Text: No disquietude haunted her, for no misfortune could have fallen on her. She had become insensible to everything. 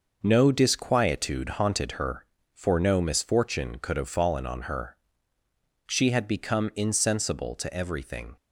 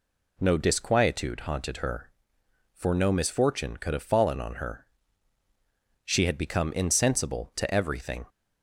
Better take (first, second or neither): second